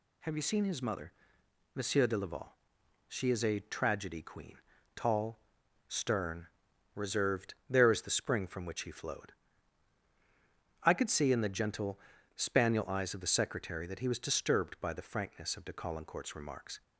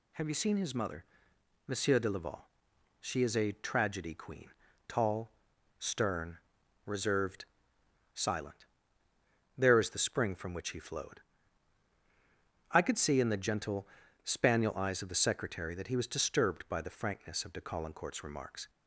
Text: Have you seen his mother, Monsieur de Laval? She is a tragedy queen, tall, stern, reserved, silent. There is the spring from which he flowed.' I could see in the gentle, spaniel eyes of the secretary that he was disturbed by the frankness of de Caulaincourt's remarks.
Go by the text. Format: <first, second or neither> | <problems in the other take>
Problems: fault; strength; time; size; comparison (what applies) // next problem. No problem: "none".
second | skips "silent"; at 7.6 s